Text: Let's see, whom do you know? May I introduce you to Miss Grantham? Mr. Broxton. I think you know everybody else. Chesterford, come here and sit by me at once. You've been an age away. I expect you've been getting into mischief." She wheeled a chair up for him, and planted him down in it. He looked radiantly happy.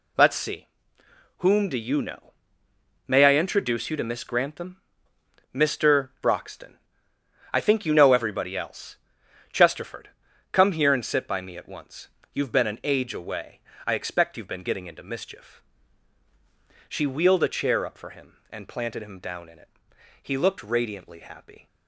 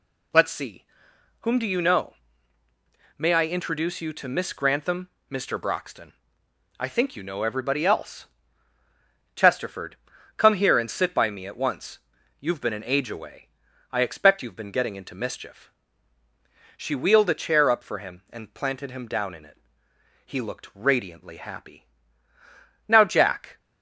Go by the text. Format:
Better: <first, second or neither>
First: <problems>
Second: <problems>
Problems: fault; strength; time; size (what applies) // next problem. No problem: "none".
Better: first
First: none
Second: goes on to say "Now Jack"; noticeable; from 22.8 s on; 0.70 s long